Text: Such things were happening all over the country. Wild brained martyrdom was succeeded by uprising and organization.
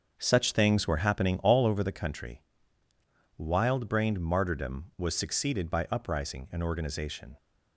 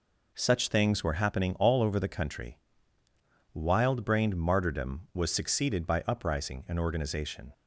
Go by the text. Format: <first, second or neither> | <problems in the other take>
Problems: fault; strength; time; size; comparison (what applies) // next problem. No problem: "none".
second | starts louder than the rest; until 1.9 s; 6.5 dB